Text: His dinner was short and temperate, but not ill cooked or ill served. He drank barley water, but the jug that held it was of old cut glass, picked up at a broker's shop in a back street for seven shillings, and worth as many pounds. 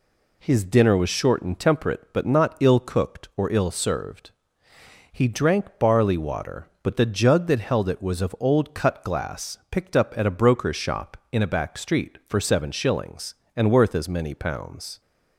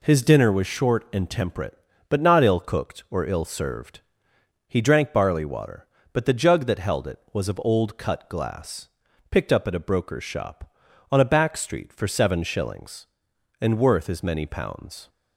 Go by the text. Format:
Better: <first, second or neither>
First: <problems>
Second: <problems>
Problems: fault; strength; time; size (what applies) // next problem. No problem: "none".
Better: first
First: none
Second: says "on" for "in"; at 11.0 s